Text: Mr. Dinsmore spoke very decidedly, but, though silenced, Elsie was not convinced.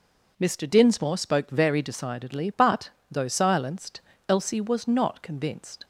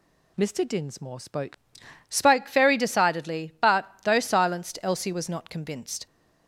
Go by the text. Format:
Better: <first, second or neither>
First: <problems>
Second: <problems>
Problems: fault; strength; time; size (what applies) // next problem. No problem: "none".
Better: first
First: none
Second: says "spoke" twice; at 2.0 s